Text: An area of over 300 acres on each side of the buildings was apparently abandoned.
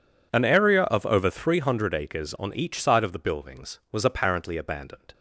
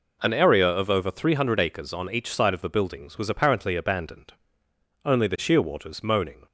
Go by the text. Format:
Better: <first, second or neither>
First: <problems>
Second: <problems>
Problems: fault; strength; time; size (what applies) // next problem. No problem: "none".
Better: first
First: none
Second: goes on to say "Only the shearwaters moaning"; from 5.0 s on; 1.4 s long